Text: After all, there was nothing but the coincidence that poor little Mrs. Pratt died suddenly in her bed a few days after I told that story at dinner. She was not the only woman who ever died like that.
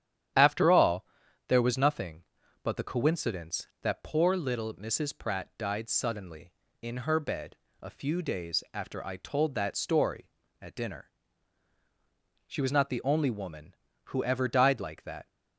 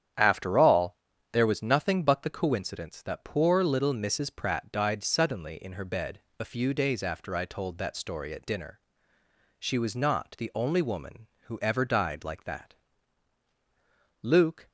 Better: first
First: starts louder than the rest; strong; until 1.7 s; 10.5 dB // pauses between "bed" and "a"; slight; at 7.5 s; 0.24 s long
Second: starts louder than the rest; strong; until 1.5 s; 9.5 dB // pauses between "bed" and "a"; slight; at 6.1 s; 0.18 s long // goes on to say "Luke"; slight; from 14.2 s on; 0.46 s long

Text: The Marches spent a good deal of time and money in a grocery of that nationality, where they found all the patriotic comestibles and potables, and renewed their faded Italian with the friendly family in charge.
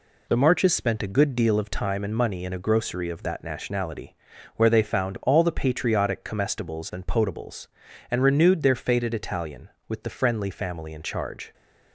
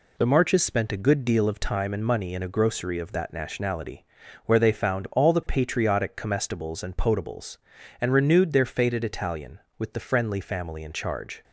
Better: neither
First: none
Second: none

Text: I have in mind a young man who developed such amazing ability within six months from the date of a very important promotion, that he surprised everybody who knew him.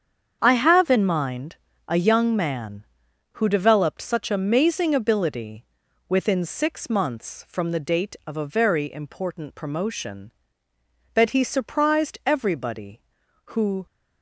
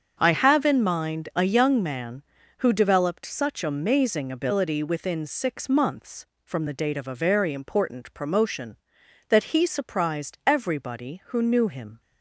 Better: second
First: starts louder than the rest; strong; until 1.4 s; 7.5 dB // pauses between "mind" and "a"; slight; at 1.5 s; 0.32 s long // pauses between "ability" and "within"; noticeable; at 5.6 s; 0.46 s long // stops before "knew him"; at 13.8 s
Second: starts louder than the rest; until 1.2 s; 7 dB

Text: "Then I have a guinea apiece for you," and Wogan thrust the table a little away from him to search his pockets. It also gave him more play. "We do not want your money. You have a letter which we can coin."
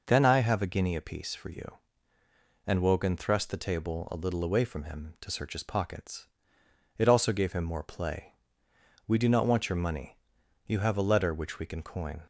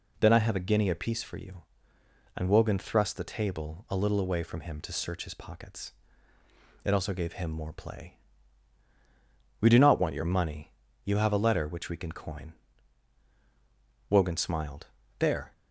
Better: first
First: none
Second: goes on to say "Wogan smiled There"; from 14.1 s on; 1.4 s long

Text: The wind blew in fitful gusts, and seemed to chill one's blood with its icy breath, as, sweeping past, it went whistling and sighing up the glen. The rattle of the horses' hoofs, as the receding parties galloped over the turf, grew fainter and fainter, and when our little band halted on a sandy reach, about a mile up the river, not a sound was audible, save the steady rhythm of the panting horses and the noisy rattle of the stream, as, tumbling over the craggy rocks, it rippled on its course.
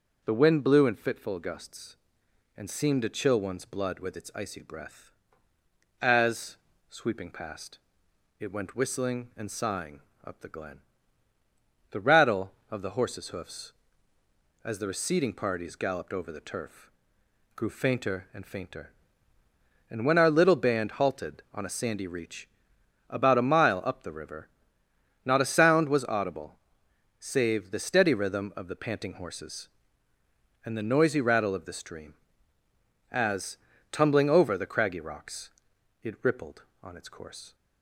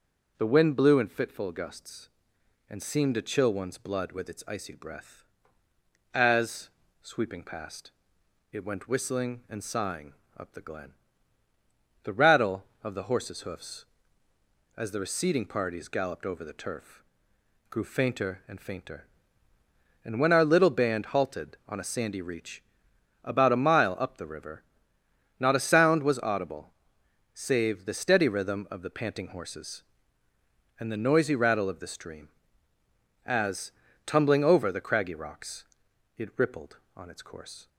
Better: neither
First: pauses between "sighing" and "up"; slight; at 9.9 s; 0.24 s long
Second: pauses between "sighing" and "up"; slight; at 10.1 s; 0.24 s long

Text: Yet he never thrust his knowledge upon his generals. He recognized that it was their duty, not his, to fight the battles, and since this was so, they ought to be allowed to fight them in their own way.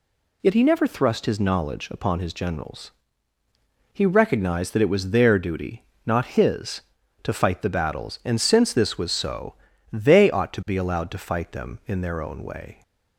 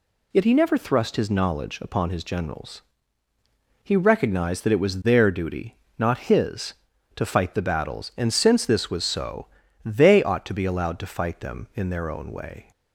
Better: neither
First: none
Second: none

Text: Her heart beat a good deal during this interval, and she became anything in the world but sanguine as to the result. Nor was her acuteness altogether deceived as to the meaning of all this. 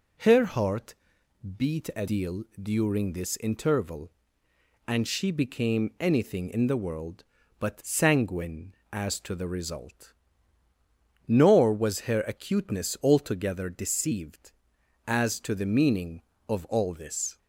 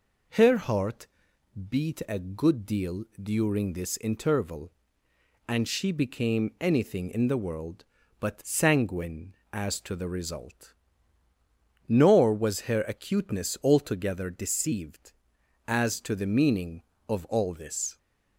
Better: second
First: pauses between "heart" and "beat"; noticeable; at 0.9 s; 0.62 s long // skips "good"; at 2.0 s // pauses between "deal" and "during"; slight; at 2.4 s; 0.16 s long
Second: pauses between "heart" and "beat"; noticeable; at 1.0 s; 0.62 s long // pauses between "deal" and "during"; slight; at 3.0 s; 0.16 s long

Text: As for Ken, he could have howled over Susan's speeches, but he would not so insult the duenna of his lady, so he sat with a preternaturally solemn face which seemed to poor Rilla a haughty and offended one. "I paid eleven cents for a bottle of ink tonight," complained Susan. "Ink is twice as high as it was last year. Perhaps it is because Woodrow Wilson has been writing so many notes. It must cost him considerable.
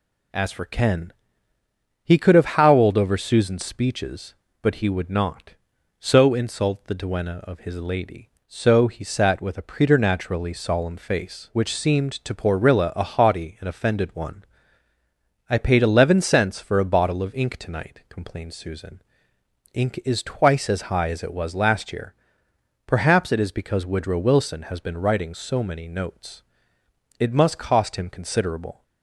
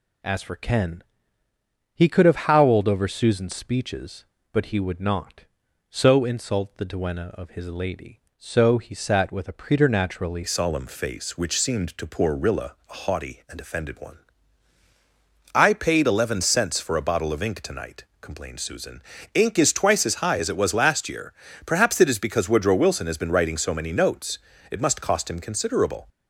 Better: first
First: none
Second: changes voice at "solemn"; from 10.4 s on; 15.6 s long // pauses between "Rilla" and "a"; slight; at 12.7 s; 0.16 s long

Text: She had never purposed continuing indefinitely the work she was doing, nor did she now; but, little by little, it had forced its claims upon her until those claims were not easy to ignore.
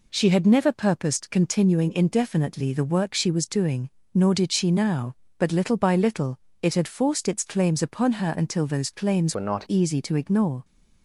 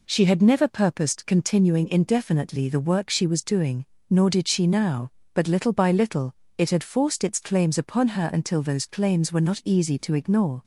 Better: second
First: changes voice from "were" to "not"; from 9.3 to 9.6 s; 0.3 s long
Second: none

